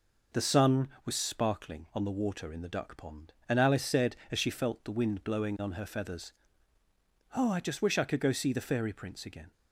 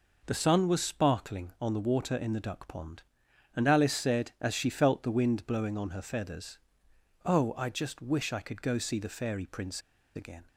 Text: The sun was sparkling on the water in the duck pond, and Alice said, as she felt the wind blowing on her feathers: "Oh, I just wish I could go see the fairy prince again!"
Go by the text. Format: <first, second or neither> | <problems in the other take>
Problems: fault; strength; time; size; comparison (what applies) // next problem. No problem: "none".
first | pauses between "prince" and "again"; slight; at 9.8 s; 0.35 s long